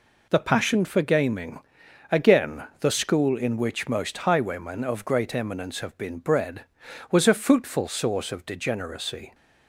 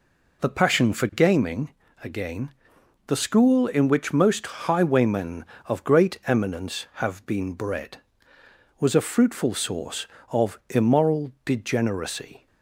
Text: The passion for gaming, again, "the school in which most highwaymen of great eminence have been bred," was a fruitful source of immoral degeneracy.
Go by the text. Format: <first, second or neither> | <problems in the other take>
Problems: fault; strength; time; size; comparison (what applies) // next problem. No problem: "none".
second | skips "immoral"; at 8.4 s